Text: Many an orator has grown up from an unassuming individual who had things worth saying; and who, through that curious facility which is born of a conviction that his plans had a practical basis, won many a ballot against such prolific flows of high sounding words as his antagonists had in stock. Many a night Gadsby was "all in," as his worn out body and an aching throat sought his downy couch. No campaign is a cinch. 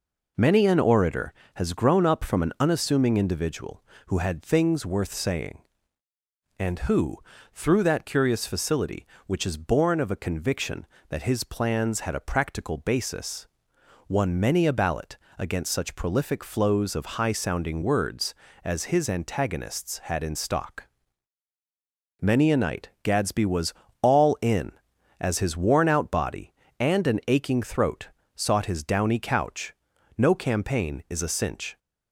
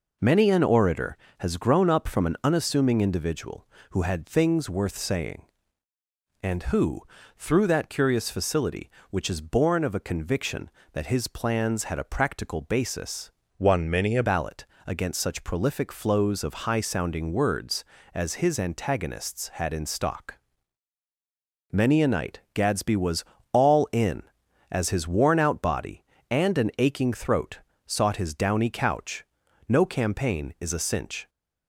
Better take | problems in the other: first | changes voice from "won" to "a"; from 13.5 to 14.2 s; 0.7 s long // pauses between "ballot" and "against"; slight; at 14.6 s; 0.20 s long; slight in the first // pauses between "was" and "all"; slight; at 23.2 s; 0.28 s long; slight in the first // pauses between "throat" and "sought"; slight; at 27.6 s; 0.26 s long; slight in the first

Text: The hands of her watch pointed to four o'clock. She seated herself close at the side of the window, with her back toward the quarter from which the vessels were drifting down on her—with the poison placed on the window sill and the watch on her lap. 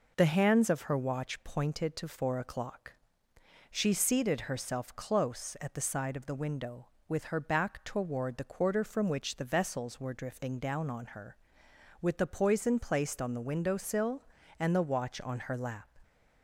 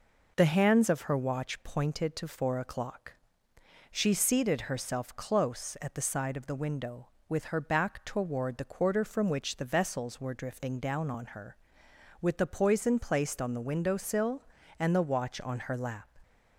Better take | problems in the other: neither | none

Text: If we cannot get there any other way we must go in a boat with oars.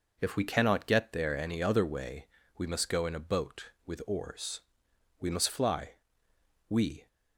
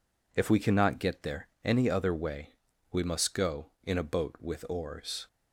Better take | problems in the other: second | pauses between "way" and "we"; slight; at 2.2 s; 0.32 s long; also in the second // goes on to say "We must fly we"; strong; from 5.1 s on; 1.8 s long

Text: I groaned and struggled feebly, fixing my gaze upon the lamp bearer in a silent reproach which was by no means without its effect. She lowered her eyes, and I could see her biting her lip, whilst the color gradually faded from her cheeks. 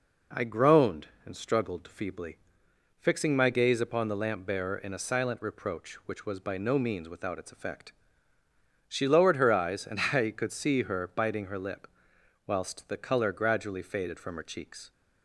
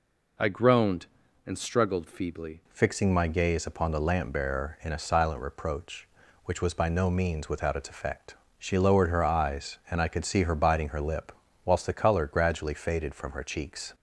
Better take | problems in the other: first | changes voice at "fixing"; from 2.7 s on; 11.2 s long

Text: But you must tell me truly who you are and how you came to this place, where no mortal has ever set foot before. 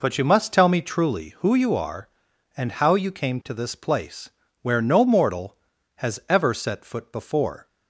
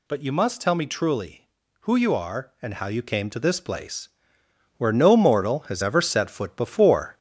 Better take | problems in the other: first | gets louder; throughout; 3.5 dB

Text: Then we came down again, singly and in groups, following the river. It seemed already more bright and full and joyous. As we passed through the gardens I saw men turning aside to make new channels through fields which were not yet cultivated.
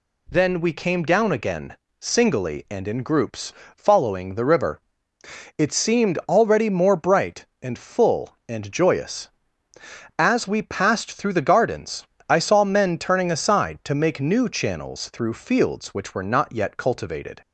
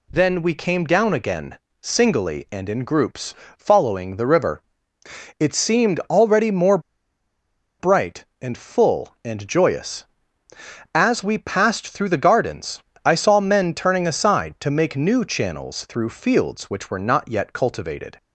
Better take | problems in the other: first | pauses between "more" and "bright"; at 6.7 s; 1.0 s long // pauses between "gardens" and "I"; slight; at 12.8 s; 0.22 s long; slight in the first

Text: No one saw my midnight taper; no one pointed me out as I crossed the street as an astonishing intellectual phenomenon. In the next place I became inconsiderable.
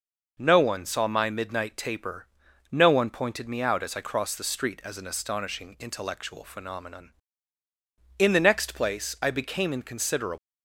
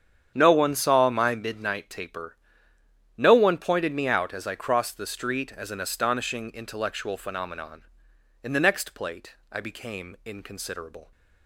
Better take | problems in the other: first | starts louder than the rest; strong; until 1.3 s; 8.5 dB // says "plate" for "place"; at 8.9 s

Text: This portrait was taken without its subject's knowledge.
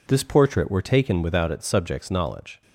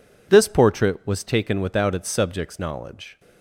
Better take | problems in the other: second | says "were" for "was"; at 0.7 s

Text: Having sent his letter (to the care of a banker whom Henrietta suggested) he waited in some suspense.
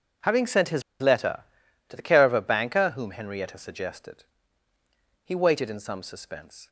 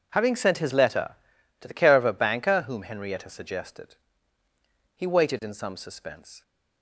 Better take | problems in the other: second | pauses between "his" and "letter"; slight; at 0.8 s; 0.17 s long

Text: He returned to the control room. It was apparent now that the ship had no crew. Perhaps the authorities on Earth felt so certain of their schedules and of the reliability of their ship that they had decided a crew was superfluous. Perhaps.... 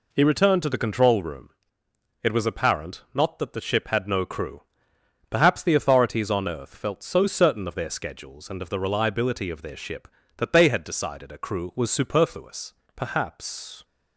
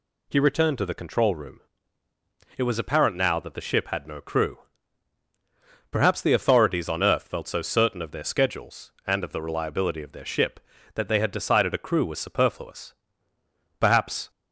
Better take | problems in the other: second | says "not" for "now"; at 3.1 s

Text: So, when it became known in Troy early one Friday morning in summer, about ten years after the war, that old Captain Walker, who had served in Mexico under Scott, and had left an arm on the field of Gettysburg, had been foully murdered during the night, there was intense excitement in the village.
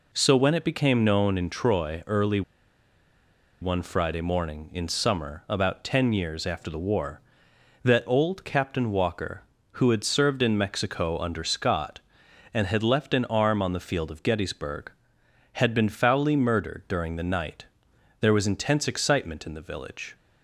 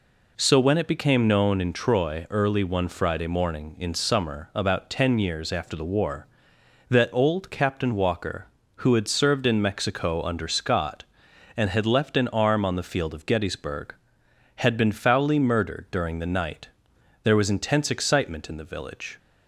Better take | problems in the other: second | pauses between "early" and "one"; at 2.4 s; 1.1 s long

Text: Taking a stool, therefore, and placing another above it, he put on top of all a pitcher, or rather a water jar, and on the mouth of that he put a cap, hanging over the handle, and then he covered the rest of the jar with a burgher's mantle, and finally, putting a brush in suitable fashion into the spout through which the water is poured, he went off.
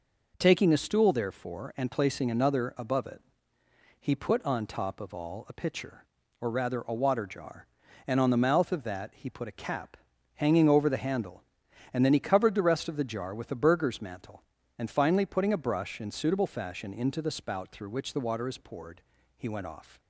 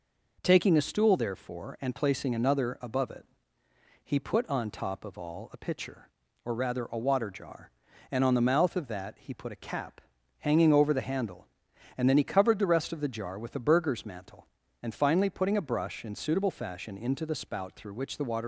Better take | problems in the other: first | stops before "is poured he went off"; at 18.4 s

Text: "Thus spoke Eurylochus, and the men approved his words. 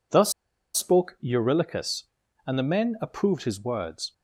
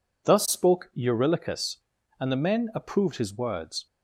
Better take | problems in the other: second | pauses between "Thus" and "spoke"; at 0.3 s; 0.42 s long

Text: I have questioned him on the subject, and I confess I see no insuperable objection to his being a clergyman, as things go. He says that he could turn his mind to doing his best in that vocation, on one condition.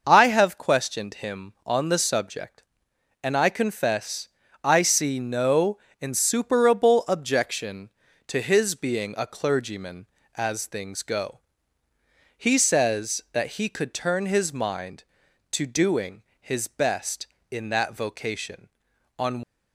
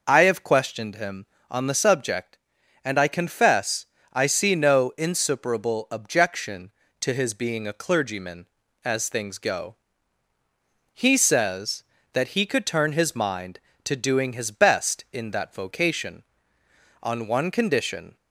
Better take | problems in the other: second | pauses between "confess" and "I"; slight; at 4.2 s; 0.36 s long; slight in the second // pauses between "no" and "insuperable"; slight; at 5.7 s; 0.24 s long // pauses between "doing" and "his"; slight; at 16.2 s; 0.18 s long // stops before "one condition"; at 19.4 s

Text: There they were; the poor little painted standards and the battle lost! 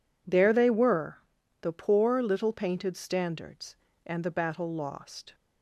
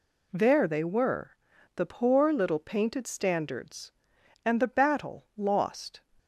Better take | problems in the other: neither | none

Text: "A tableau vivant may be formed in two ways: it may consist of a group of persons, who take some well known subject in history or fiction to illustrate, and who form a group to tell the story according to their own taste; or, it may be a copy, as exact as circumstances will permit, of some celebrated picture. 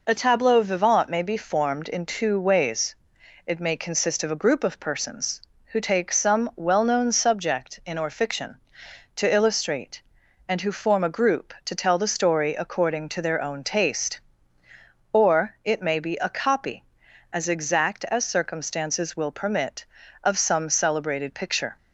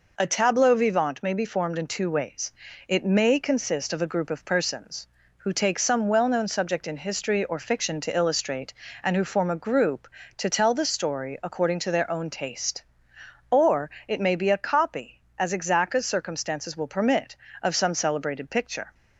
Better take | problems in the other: second | skips "history"; at 7.9 s

